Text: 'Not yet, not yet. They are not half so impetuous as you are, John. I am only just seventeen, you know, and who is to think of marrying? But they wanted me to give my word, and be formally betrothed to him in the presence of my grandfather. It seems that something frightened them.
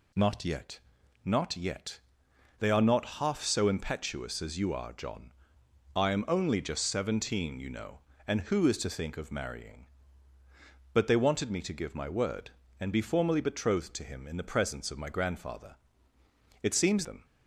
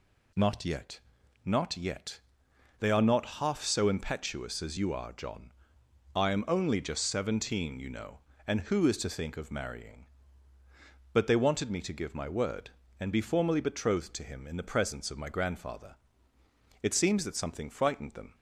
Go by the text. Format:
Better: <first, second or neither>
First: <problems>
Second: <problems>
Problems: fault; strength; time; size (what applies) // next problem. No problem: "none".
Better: second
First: skips "that something frightened"; at 17.0 s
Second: none